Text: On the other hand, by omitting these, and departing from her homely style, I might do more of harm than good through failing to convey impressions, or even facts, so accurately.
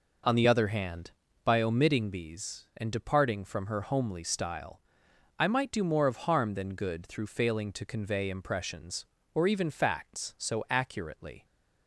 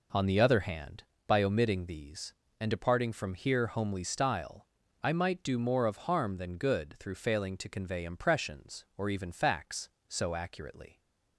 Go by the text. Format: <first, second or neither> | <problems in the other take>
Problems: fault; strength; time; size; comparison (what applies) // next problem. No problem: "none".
first | says "here" for "her"; at 3.3 s